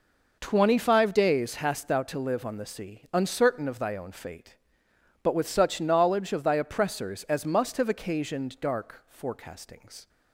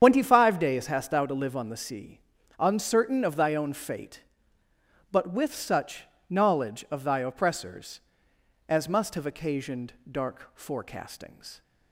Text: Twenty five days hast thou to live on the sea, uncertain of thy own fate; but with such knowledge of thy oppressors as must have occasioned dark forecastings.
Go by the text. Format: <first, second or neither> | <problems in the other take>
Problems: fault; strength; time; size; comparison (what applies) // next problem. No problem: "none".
first | loses the start of "Twenty"; at 0.0 s; 100 ms // starts louder than the rest; strong; until 1.0 s; 8 dB // pauses between "such" and "knowledge"; slight; at 6.0 s; 0.26 s long // pauses between "occasioned" and "dark"; slight; at 9.9 s; 0.18 s long